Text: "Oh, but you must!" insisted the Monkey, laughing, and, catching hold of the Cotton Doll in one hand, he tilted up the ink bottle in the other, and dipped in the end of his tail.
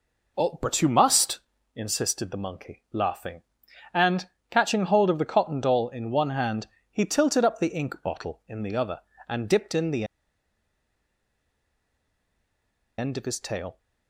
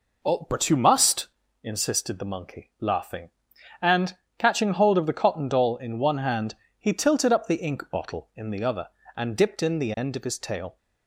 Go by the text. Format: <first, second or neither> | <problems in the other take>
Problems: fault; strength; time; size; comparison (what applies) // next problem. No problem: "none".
second | pauses between "the" and "end"; strong; at 10.0 s; 2.9 s long